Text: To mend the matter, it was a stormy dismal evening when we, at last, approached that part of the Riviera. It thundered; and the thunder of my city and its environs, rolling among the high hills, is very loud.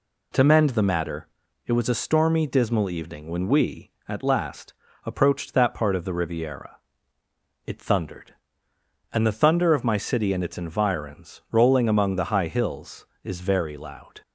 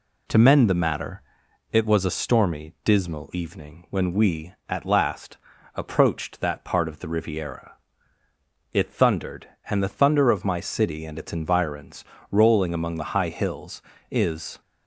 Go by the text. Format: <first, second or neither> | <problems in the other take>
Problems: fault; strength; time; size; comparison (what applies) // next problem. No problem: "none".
first | stops before "very loud"; at 14.6 s